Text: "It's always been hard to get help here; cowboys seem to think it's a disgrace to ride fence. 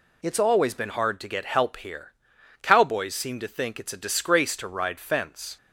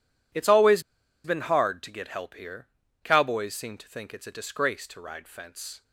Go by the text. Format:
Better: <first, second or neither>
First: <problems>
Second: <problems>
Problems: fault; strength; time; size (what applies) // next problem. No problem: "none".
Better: first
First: none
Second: pauses between "always" and "been"; at 0.8 s; 0.43 s long